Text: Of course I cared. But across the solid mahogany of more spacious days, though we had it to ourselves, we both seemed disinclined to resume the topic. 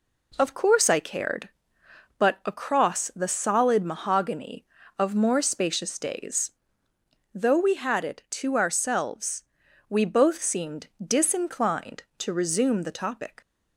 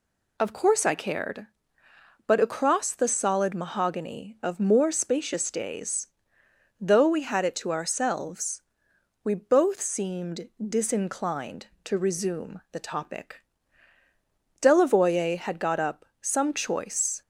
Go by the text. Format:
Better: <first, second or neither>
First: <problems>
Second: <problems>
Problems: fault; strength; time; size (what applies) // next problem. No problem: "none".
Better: first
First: pauses between "seemed" and "disinclined"; slight; at 10.8 s; 0.18 s long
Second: pauses between "seemed" and "disinclined"; slight; at 10.4 s; 0.18 s long // goes on to say "Delavoye had got up some choice"; strong; from 14.6 s on; 2.6 s long